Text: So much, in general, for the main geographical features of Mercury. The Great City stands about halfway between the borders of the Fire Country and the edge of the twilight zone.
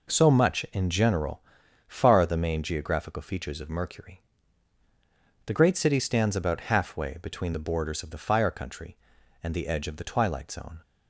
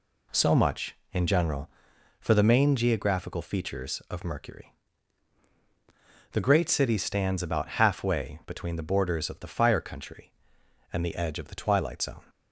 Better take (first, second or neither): second